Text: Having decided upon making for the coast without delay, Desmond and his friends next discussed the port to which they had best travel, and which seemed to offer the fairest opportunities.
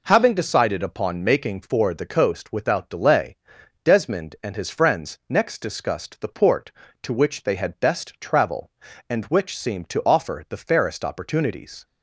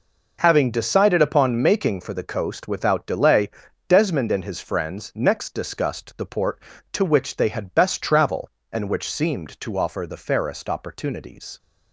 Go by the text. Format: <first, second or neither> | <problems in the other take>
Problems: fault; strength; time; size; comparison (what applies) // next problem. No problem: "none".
neither | none